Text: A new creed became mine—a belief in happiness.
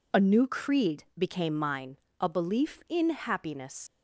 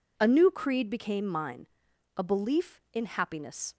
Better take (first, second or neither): second